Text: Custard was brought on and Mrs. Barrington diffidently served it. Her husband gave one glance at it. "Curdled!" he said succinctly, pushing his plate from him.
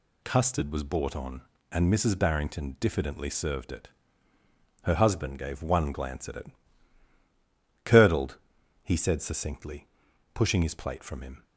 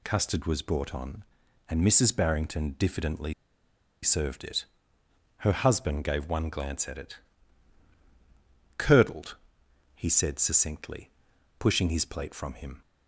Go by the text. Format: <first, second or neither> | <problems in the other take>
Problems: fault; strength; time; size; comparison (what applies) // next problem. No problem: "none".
first | pauses between "diffidently" and "served"; noticeable; at 3.3 s; 0.69 s long